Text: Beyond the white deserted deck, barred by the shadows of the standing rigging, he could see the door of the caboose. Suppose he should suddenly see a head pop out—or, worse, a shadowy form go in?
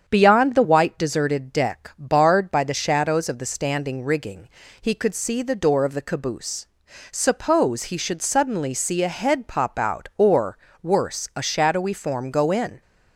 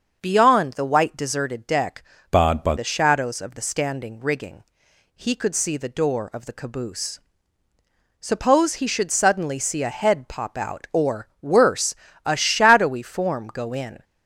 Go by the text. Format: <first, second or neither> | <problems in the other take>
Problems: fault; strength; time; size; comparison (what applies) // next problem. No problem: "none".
first | starts louder than the rest; until 1.2 s; 6.5 dB; strong in the first // changes voice from "barred" to "by"; from 2.3 to 2.7 s; 0.4 s long